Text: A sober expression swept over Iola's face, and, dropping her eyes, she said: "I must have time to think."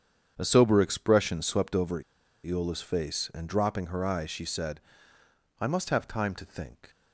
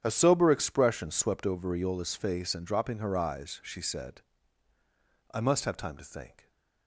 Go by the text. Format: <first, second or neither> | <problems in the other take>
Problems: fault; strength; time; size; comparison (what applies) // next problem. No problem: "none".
second | starts louder than the rest; strong; until 1.3 s; 8 dB; strong in the second // pauses between "over" and "Iola's"; at 2.0 s; 0.42 s long